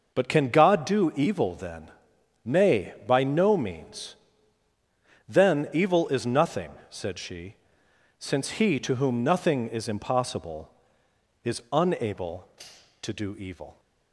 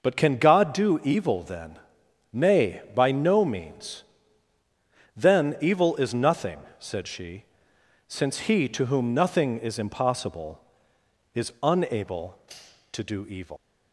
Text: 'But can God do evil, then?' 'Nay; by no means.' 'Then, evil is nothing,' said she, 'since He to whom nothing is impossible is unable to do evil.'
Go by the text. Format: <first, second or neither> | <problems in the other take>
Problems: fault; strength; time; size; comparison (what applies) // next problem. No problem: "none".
first | leaves "evil" unfinished; at 13.5 s; 130 ms